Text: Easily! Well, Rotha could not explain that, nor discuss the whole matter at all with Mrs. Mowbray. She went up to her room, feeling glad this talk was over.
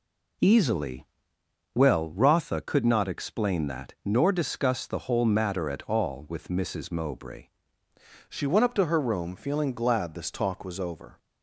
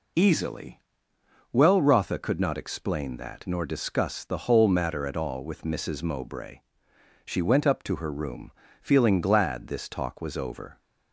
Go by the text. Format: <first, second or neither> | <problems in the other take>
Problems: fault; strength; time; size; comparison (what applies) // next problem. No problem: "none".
second | changes voice at "She"; from 8.2 s on; 2.9 s long